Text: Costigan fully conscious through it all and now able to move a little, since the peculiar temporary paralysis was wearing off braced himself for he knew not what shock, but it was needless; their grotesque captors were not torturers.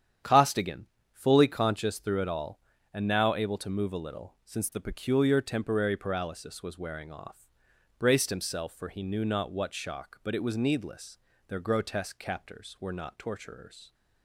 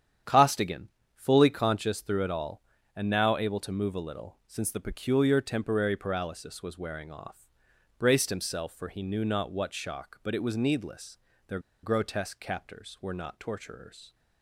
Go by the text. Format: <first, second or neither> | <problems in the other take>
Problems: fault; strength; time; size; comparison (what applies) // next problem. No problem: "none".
first | starts louder than the rest; strong; until 1.5 s; 9 dB; strong in the first // pauses between "Costigan" and "fully"; slight; at 0.8 s; 0.28 s long; slight in the first // pauses between "off" and "braced"; noticeable; at 7.4 s; 0.50 s long; noticeable in the first // pauses between "their" and "grotesque"; slight; at 11.5 s; 0.23 s long